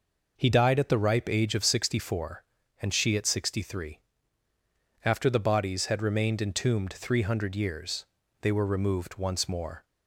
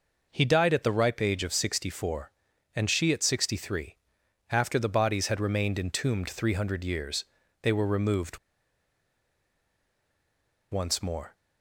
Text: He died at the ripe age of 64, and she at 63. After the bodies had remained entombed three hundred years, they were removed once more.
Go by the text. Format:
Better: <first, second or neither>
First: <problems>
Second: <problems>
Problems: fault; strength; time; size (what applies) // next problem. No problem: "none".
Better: first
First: none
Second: pauses between "removed" and "once"; strong; at 8.3 s; 2.3 s long